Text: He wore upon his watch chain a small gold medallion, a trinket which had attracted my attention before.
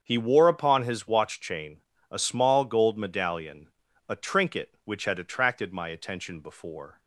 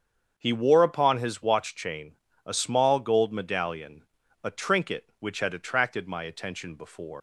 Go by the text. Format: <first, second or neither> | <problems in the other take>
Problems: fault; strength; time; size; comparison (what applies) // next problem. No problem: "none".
first | starts louder than the rest; strong; until 1.3 s; 7.5 dB; strong in the first // pauses between "chain" and "a"; slight; at 2.1 s; 0.28 s long; slight in the first // leaves "before" unfinished; at 7.1 s; 145 ms